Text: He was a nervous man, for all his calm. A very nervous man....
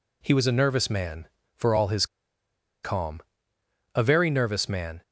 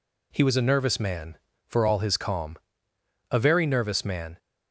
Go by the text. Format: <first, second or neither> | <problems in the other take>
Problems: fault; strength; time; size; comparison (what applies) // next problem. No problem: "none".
second | pauses between "his" and "calm"; noticeable; at 2.0 s; 0.78 s long